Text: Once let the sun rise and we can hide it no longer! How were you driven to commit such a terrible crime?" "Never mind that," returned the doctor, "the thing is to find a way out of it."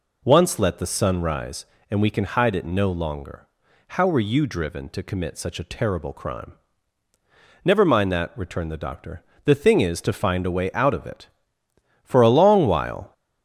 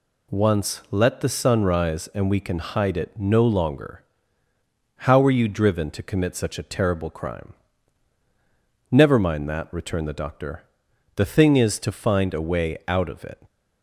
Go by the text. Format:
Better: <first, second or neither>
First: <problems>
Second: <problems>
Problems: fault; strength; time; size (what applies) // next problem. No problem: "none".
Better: second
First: goes on to say "For a long while"; noticeable; from 12.0 s on; 1.0 s long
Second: none